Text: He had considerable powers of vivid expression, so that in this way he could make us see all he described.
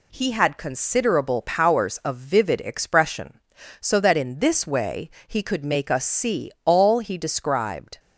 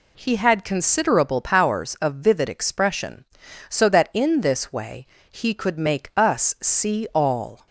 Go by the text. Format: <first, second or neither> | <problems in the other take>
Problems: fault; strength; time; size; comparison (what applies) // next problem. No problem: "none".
first | pauses between "way" and "he"; slight; at 5.0 s; 0.24 s long; slight in the first // stops before "he described"; at 7.6 s